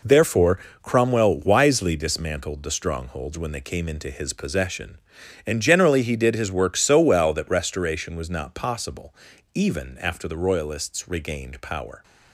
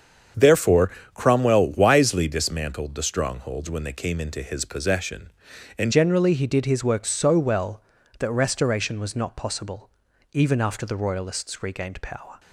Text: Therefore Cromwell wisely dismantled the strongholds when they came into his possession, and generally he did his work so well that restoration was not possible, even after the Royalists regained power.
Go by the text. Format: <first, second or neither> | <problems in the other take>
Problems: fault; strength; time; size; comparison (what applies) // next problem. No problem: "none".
first | starts louder than the rest; strong; until 1.5 s; 7 dB // pauses between "Therefore" and "Cromwell"; slight; at 0.9 s; 0.22 s long; slight in the first // changes voice at "generally"; from 5.9 s on; 6.4 s long